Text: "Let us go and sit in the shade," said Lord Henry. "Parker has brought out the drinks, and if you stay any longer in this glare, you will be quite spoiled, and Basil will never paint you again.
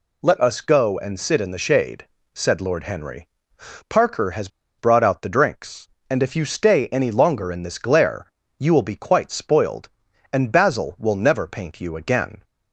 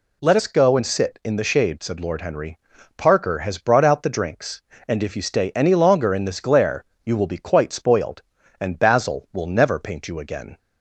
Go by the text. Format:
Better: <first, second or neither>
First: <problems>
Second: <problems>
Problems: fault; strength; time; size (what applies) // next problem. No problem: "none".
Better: second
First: pauses between "has" and "brought"; slight; at 4.4 s; 0.31 s long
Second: none